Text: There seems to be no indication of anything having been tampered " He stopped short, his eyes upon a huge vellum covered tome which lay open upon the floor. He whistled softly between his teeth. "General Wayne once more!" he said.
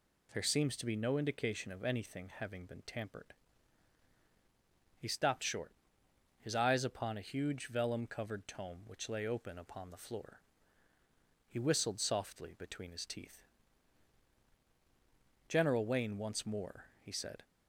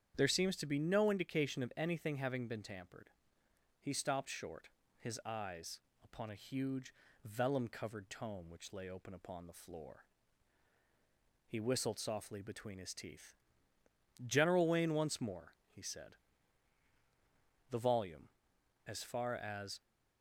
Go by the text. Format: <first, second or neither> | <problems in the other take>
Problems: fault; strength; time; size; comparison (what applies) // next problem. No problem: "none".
first | starts louder than the rest; strong; until 1.1 s; 8.5 dB // pauses between "eyes" and "upon"; slight; at 5.8 s; 0.20 s long // pauses between "huge" and "vellum"; slight; at 6.9 s; 0.32 s long // goes on to say "The volume as far as"; strong; from 17.7 s on; 2.1 s long